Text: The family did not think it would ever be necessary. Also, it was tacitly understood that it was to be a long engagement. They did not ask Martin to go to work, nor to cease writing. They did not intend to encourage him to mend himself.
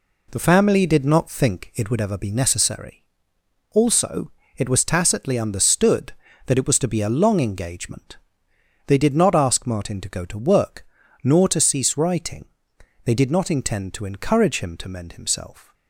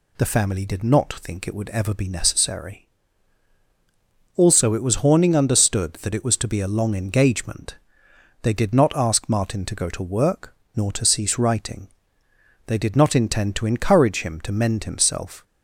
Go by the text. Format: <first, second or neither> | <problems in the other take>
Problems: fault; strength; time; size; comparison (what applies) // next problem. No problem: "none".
first | says "horning" for "tacitly"; at 4.9 s